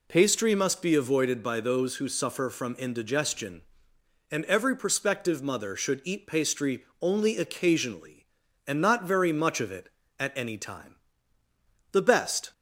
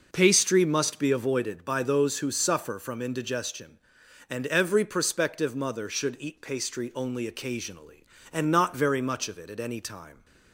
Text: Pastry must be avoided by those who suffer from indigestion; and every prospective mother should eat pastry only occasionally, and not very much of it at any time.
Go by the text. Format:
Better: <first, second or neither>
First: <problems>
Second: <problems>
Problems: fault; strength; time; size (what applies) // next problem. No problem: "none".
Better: second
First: pauses between "pastry" and "only"; slight; at 6.8 s; 0.16 s long // goes on to say "The best"; from 11.9 s on; 0.60 s long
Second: none